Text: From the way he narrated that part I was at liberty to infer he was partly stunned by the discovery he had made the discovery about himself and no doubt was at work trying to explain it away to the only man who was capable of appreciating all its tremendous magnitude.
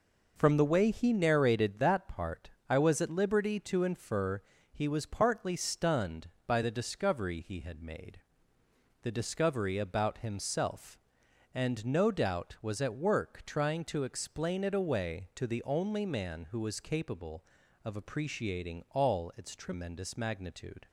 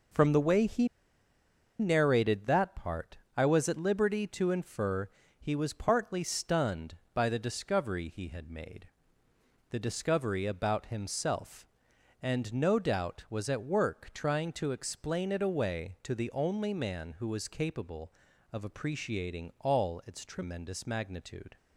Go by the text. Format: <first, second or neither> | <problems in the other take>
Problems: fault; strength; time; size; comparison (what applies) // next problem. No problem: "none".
first | pauses between "he" and "narrated"; noticeable; at 0.8 s; 0.92 s long // pauses between "part" and "I"; slight; at 3.1 s; 0.18 s long; slight in the first // pauses between "infer" and "he"; slight; at 5.1 s; 0.28 s long; slight in the first // pauses between "made" and "the"; noticeable; at 8.8 s; 0.82 s long; noticeable in the first